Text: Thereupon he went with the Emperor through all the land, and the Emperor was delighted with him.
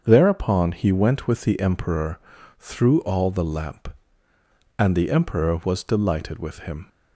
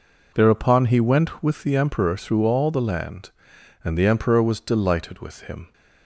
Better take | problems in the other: second | starts louder than the rest; until 1.0 s; 7 dB // pauses between "Emperor" and "through"; at 2.1 s; 0.40 s long // says "lamp" for "land"; at 3.4 s

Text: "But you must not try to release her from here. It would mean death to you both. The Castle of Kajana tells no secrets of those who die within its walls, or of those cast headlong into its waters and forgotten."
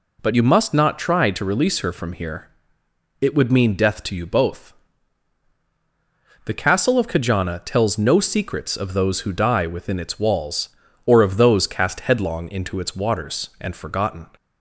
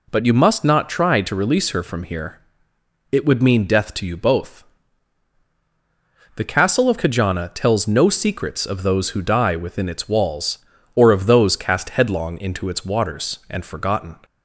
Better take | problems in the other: neither | none

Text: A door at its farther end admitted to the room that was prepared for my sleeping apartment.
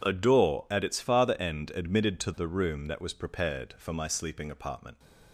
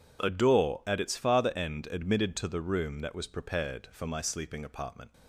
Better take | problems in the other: neither | none

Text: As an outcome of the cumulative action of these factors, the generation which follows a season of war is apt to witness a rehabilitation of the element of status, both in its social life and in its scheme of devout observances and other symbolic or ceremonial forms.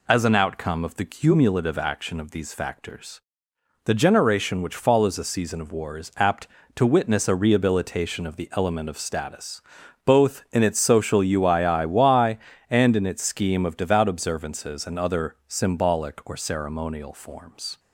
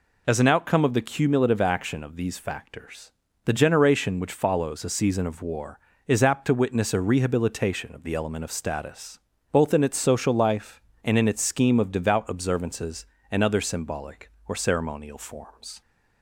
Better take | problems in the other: second | says "uiiy" for "life"; at 11.2 s

